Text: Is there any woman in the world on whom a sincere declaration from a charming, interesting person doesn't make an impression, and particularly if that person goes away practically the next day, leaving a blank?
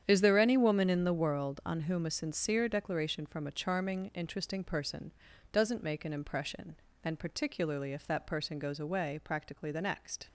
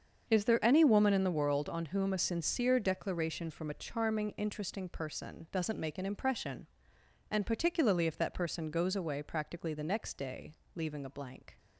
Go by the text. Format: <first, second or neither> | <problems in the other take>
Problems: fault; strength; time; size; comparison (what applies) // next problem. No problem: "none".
second | starts louder than the rest; strong; until 1.0 s; 9 dB; also in the second // pauses between "person" and "doesn't"; at 5.1 s; 0.40 s long // stops before "day leaving a blank"; at 10.2 s